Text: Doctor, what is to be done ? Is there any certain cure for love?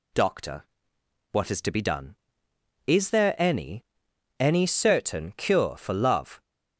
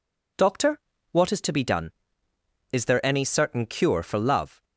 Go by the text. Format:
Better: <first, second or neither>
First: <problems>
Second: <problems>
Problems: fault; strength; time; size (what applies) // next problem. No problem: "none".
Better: second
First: says "any" twice; at 4.3 s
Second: none